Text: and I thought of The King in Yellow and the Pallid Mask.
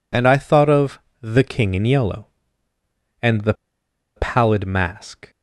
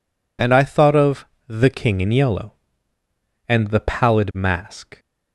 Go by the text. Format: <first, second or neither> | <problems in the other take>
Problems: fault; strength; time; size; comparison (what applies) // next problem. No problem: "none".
second | pauses between "of" and "The"; slight; at 0.9 s; 0.22 s long; slight in the second // pauses between "the" and "Pallid"; noticeable; at 3.5 s; 0.62 s long